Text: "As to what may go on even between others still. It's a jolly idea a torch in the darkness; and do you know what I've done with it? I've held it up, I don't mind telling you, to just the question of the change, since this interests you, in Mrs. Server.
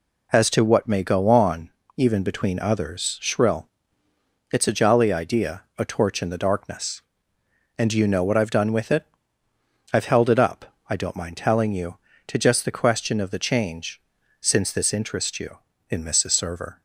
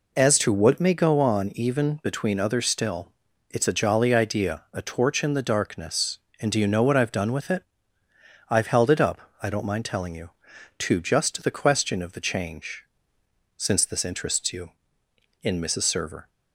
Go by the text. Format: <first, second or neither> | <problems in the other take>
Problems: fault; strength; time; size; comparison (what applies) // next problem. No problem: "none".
second | pauses between "on" and "even"; slight; at 1.7 s; 0.26 s long // says "shrill" for "still"; at 3.2 s